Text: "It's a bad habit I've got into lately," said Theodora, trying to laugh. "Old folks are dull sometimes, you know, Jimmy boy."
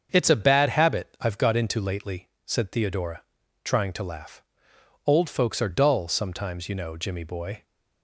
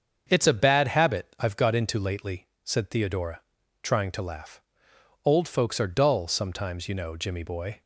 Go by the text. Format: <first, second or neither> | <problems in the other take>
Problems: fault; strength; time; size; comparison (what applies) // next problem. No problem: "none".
neither | starts louder than the rest; the same in both